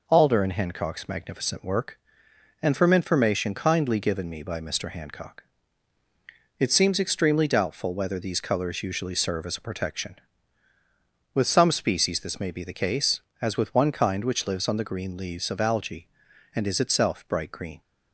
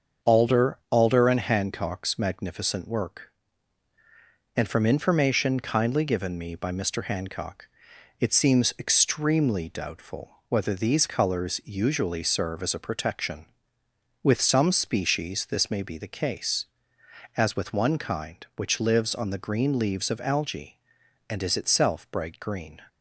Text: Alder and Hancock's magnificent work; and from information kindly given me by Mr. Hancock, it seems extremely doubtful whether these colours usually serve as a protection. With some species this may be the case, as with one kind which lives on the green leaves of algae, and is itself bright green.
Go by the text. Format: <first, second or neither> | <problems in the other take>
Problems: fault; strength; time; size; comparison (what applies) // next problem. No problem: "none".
first | starts louder than the rest; until 1.3 s; 7 dB // says "Alder" twice; at 0.9 s // pauses between "doubtful" and "whether"; slight; at 10.2 s; 0.18 s long